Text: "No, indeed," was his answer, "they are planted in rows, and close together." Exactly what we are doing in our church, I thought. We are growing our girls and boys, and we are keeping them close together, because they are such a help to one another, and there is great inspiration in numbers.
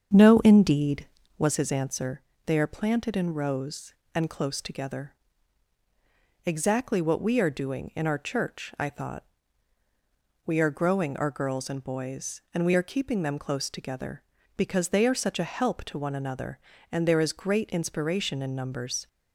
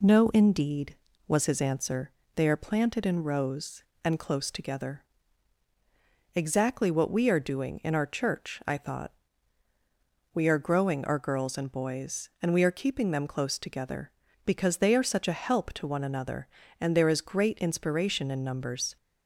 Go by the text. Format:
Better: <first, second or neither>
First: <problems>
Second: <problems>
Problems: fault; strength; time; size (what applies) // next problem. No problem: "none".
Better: second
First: starts louder than the rest; strong; until 1.5 s; 7.5 dB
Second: none